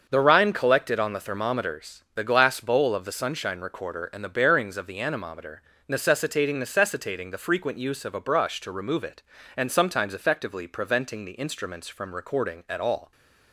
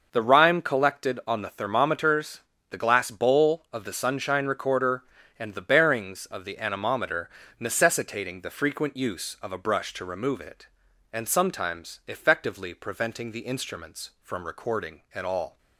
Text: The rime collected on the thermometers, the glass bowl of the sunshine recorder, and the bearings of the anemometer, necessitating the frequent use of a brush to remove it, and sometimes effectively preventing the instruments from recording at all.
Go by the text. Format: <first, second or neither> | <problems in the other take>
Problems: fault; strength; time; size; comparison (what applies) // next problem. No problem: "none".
second | starts louder than the rest; until 1.1 s; 6.5 dB; also in the second // says "necessitating" twice; at 6.5 s